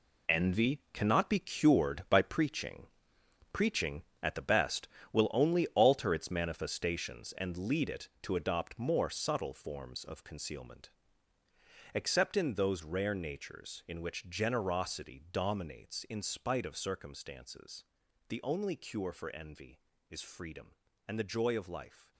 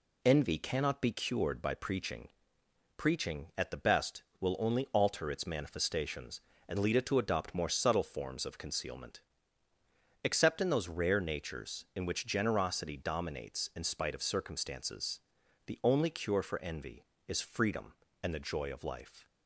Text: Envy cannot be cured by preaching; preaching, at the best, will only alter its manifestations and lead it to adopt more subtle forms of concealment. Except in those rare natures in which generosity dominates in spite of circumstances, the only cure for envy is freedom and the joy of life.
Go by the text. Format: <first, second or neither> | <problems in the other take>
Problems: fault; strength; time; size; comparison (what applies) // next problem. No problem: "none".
second | gets quieter; strong; throughout; 11 dB